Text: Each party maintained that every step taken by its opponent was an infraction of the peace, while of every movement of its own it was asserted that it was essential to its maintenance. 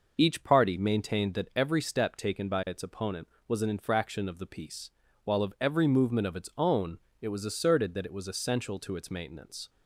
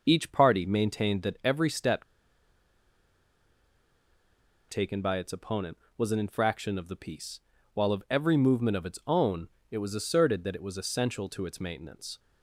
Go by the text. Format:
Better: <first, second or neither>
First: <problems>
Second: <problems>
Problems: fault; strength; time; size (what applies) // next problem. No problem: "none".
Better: first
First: pauses between "own" and "it"; slight; at 6.9 s; 0.24 s long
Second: pauses between "step" and "taken"; strong; at 2.0 s; 2.6 s long // pauses between "own" and "it"; slight; at 9.4 s; 0.24 s long